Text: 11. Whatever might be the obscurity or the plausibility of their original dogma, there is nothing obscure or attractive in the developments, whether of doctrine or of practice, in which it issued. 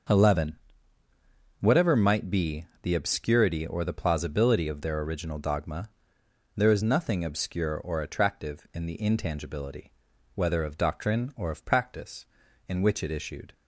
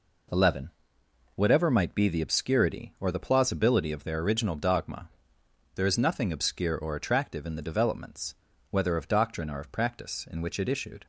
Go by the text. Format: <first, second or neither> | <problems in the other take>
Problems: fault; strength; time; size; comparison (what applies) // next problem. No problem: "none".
second | starts louder than the rest; until 2.1 s; 6.5 dB // pauses between "be" and "the"; slight; at 2.6 s; 0.18 s long // says "intangibility" for "developments"; at 9.0 s